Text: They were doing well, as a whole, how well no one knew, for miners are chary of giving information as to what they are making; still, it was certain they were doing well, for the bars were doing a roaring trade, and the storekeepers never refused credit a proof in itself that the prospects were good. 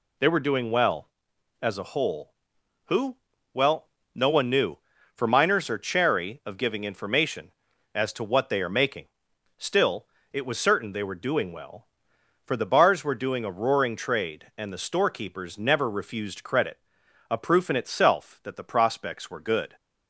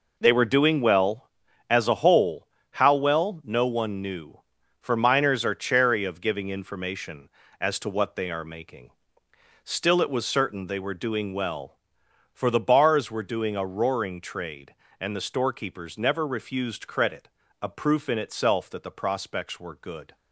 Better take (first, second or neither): second